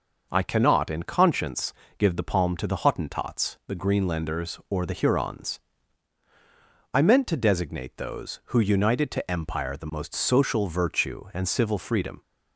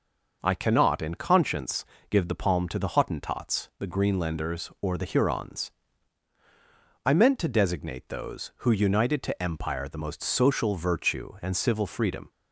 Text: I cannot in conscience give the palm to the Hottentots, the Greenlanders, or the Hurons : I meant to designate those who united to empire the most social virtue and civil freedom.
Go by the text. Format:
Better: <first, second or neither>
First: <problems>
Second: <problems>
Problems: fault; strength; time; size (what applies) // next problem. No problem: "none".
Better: neither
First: pauses between "conscience" and "give"; slight; at 1.7 s; 0.26 s long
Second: pauses between "conscience" and "give"; slight; at 1.8 s; 0.26 s long